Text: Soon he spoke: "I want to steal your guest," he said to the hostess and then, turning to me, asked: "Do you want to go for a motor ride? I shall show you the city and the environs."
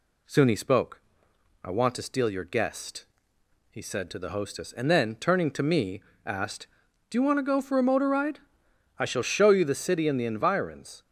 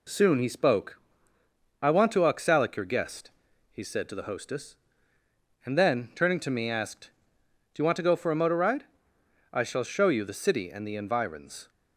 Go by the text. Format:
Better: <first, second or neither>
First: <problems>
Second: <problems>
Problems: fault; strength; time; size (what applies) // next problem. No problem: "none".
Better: first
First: none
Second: says "oxalic" for "steal"; at 2.2 s